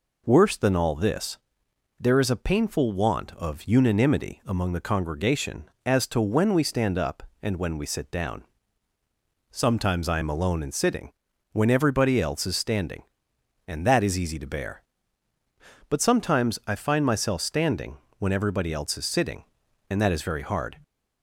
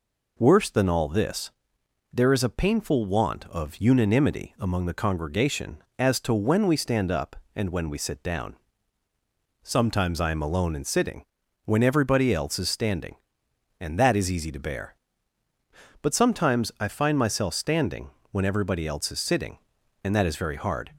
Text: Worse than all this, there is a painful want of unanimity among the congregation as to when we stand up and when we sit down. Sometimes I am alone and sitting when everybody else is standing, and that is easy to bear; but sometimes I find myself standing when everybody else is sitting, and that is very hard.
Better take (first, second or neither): neither